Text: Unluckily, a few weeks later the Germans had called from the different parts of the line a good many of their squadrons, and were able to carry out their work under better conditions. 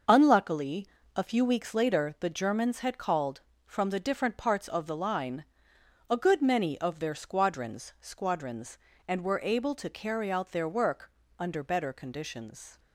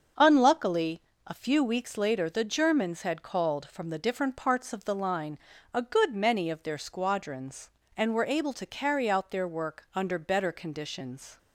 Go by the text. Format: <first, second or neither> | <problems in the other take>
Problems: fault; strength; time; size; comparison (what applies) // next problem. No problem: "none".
second | starts louder than the rest; until 1.3 s; 6 dB; also in the second // pauses between "line" and "a"; noticeable; at 5.4 s; 0.66 s long; slight in the second // says "squadrons" twice; at 8.0 s // pauses between "work" and "under"; slight; at 11.0 s; 0.30 s long